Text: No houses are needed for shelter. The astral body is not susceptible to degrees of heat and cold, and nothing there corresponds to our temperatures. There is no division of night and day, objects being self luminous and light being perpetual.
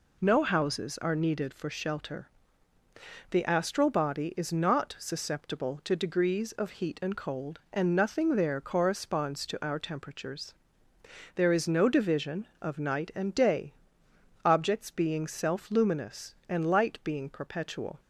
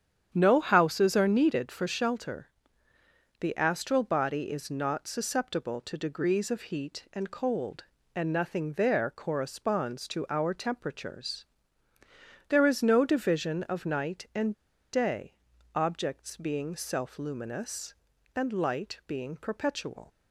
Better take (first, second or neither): first